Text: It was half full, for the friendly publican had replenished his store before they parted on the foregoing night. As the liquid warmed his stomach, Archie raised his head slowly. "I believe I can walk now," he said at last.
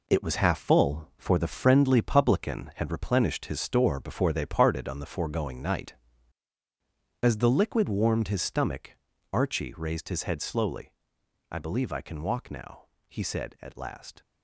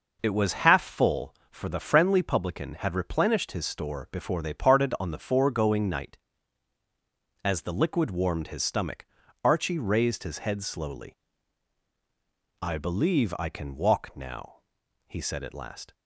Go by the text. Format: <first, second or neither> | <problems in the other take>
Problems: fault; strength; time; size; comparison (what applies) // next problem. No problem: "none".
second | gets quieter; strong; throughout; 8 dB